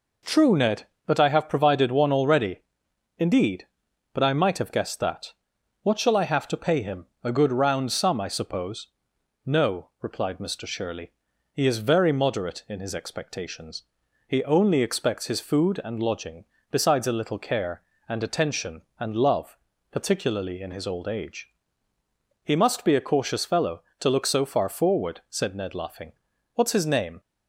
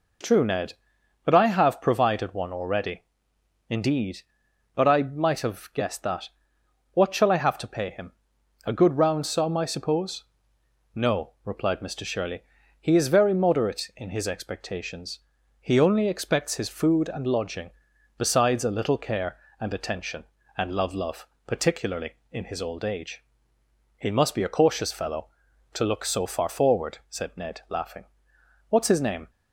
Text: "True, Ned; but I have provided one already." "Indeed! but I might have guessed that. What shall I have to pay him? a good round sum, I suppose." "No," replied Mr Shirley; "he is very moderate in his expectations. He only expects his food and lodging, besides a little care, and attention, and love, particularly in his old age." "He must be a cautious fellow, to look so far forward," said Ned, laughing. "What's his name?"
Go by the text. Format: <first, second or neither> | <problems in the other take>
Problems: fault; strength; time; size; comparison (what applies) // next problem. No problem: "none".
first | says "love" twice; at 20.9 s